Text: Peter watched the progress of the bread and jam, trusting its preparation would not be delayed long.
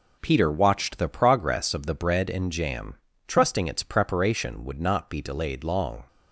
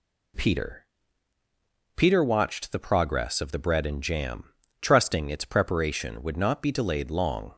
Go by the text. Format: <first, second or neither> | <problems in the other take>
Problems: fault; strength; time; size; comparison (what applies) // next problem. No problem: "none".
first | says "Peter" twice; at 1.9 s